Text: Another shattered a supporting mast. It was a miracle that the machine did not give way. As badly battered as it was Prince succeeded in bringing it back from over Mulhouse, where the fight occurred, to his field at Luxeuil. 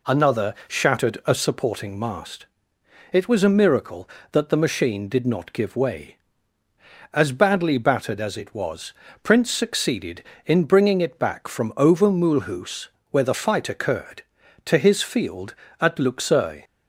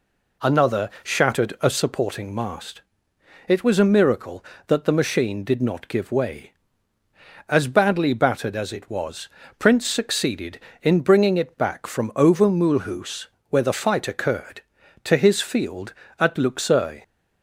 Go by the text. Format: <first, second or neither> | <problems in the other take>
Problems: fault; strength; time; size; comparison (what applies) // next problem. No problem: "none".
neither | pauses between "was" and "Prince"; slight; the same in both